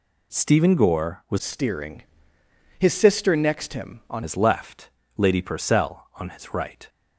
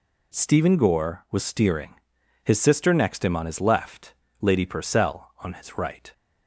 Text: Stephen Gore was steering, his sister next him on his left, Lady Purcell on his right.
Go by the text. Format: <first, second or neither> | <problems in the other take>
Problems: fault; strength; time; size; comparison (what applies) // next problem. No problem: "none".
second | changes voice from "steering" to "on"; from 1.3 to 4.2 s; 2.9 s long